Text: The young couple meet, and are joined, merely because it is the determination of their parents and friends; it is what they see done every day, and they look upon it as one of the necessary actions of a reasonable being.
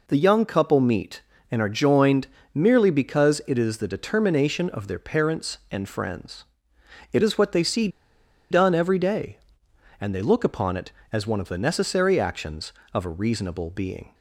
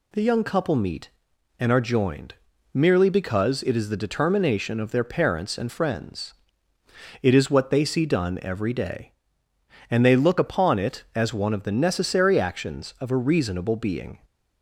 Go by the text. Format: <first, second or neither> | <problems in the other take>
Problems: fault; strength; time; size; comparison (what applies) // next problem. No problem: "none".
second | pauses between "see" and "done"; noticeable; at 7.8 s; 0.62 s long